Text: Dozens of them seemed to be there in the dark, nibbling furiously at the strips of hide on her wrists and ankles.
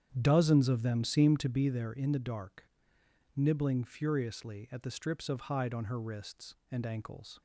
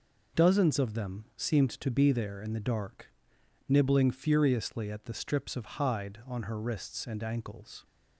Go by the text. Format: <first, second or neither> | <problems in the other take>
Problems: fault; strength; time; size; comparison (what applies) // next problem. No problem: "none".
second | starts louder than the rest; strong; until 1.7 s; 9 dB